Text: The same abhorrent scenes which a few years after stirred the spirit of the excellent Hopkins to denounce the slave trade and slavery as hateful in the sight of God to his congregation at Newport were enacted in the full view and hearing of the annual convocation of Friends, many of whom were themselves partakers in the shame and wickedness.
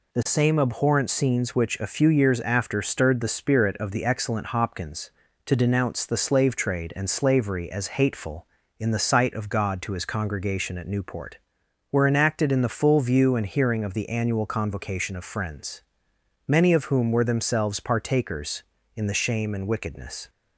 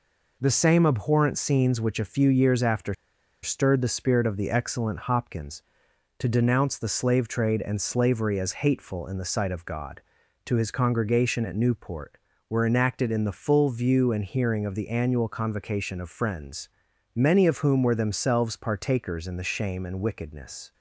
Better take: first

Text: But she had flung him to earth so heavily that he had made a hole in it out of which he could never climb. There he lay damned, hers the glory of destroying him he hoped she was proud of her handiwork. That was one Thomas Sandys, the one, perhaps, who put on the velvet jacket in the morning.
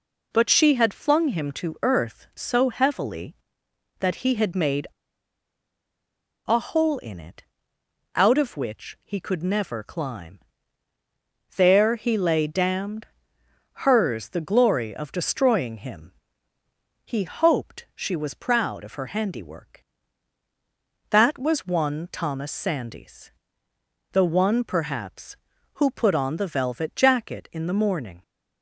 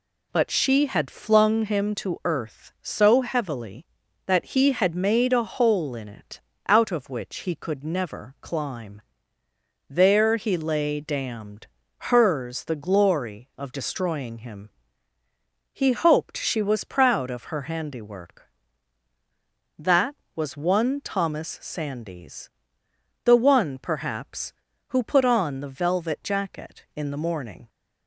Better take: second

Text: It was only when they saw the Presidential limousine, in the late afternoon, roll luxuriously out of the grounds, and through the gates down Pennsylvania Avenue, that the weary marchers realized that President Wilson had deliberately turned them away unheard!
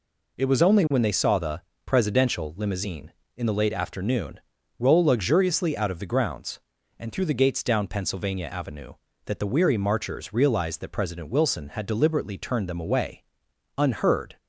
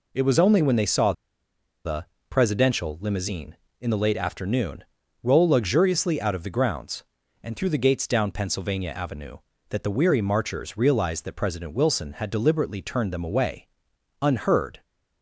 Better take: first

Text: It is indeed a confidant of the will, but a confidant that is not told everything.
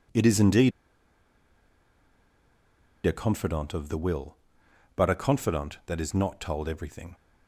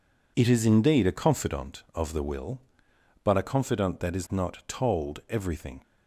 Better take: second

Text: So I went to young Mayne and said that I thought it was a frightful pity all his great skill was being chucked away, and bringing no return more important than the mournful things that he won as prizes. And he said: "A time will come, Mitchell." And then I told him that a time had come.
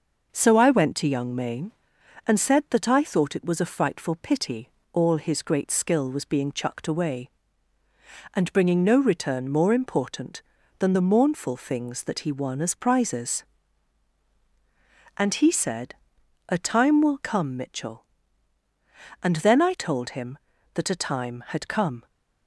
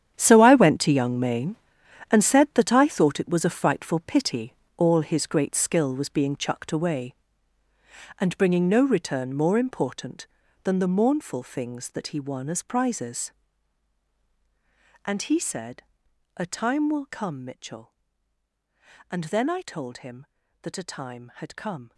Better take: first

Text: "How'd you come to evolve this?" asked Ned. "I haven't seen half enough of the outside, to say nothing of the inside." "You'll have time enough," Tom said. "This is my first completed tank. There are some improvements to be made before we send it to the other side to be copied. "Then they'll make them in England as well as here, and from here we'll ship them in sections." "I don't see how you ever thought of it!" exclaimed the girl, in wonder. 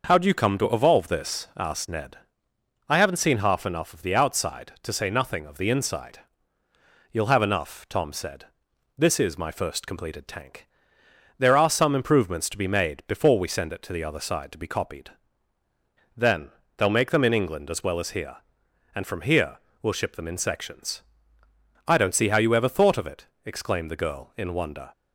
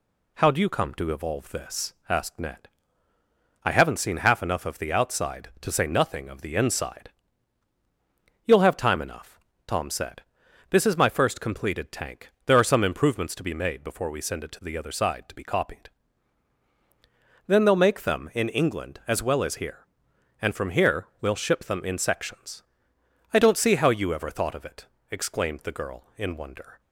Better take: second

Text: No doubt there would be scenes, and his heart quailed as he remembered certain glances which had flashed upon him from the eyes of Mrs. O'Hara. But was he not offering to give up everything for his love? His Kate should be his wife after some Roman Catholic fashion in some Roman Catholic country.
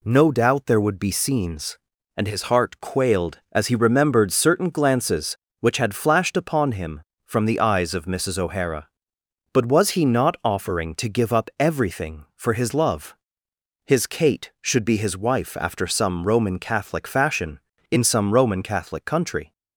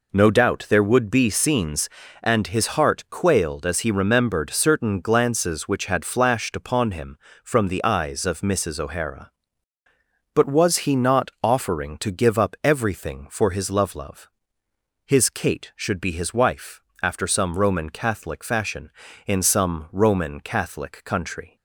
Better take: first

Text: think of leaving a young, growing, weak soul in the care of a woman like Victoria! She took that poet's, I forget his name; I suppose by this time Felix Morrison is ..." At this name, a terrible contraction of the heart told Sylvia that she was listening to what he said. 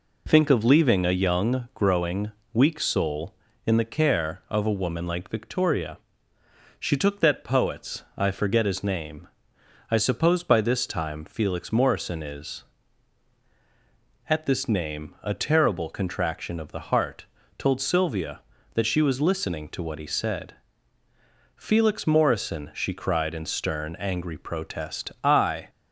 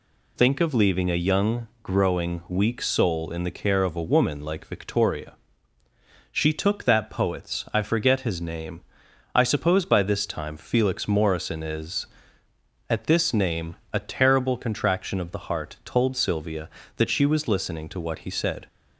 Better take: second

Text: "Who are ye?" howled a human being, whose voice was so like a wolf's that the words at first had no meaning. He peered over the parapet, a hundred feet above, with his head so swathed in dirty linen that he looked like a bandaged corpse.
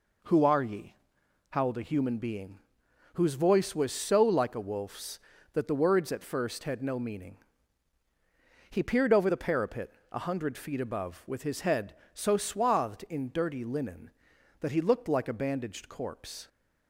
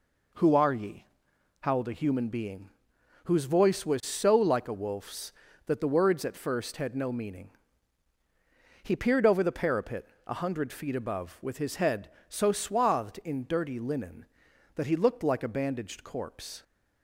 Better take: neither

